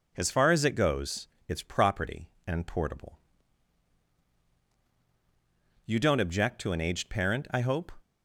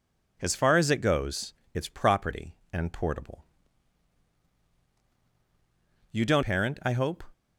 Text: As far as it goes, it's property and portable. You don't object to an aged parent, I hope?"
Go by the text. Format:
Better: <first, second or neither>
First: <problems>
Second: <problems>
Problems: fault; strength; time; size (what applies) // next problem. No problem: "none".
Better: first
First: none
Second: skips "object to an aged"; at 6.4 s